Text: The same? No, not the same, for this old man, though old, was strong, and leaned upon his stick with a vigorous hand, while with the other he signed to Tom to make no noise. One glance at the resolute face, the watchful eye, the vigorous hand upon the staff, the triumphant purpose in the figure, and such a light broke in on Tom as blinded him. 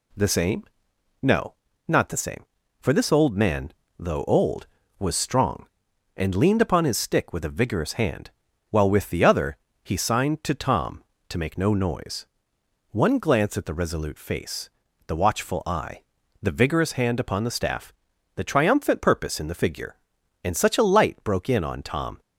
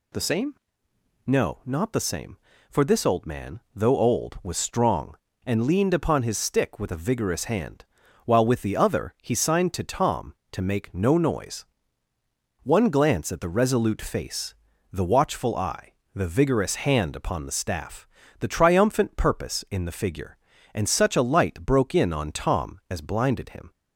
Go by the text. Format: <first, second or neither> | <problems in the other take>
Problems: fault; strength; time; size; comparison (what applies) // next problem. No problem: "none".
second | pauses between "other" and "he"; slight; at 9.5 s; 0.26 s long // stops before "as blinded him"; at 22.2 s